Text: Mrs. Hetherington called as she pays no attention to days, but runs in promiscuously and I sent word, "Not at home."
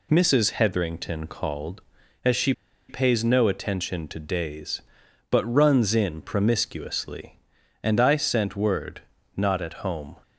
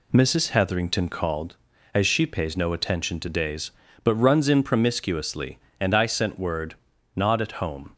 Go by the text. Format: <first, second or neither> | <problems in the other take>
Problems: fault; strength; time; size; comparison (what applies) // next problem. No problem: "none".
second | pauses between "she" and "pays"; at 2.5 s; 0.37 s long